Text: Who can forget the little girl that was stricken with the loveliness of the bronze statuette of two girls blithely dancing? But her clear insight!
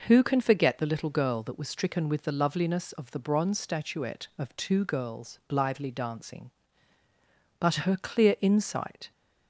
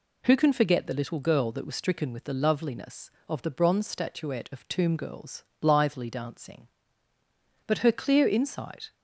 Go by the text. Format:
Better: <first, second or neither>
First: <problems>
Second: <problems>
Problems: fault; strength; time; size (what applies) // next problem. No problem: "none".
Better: first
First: none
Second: says "tomb" for "two"; at 4.6 s // pauses between "girls" and "blithely"; slight; at 5.4 s; 0.16 s long